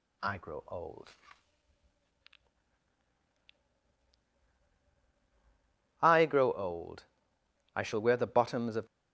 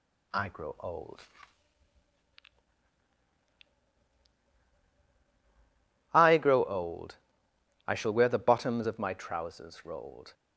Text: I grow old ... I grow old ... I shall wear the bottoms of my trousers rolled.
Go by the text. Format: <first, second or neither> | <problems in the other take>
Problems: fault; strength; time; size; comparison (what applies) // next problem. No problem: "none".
second | stops before "my trousers rolled"; at 8.8 s